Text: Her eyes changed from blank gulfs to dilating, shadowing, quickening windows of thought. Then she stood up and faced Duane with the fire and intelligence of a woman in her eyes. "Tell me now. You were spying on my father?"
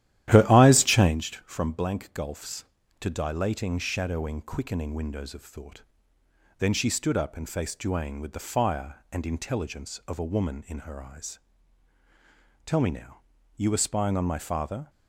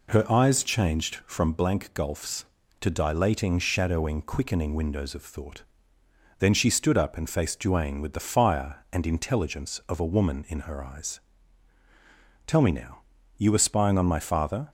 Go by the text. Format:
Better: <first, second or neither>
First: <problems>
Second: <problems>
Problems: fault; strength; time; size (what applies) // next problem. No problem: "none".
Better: second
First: starts louder than the rest; strong; until 1.2 s; 12.5 dB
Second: none